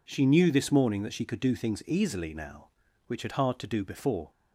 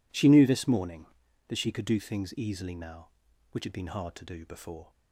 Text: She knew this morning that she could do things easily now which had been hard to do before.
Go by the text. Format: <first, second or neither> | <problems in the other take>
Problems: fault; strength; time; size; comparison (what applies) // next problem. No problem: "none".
second | skips "been"; at 3.3 s